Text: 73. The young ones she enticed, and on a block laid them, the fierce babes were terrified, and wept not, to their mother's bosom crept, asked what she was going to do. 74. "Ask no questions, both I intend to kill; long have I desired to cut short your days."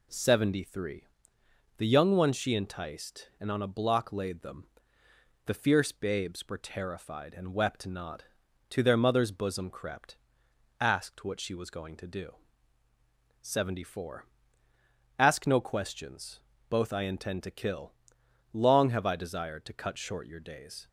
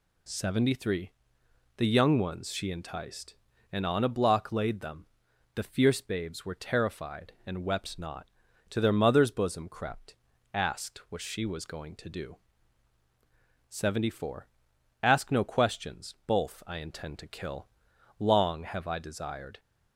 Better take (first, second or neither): first